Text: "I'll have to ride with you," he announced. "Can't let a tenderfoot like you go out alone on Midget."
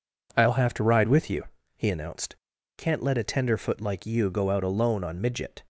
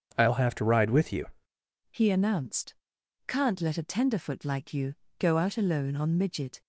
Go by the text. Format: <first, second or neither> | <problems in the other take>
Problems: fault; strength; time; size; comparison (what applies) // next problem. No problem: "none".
first | changes voice at "he"; from 1.9 s on; 4.7 s long // pauses between "you" and "go"; slight; at 4.9 s; 0.24 s long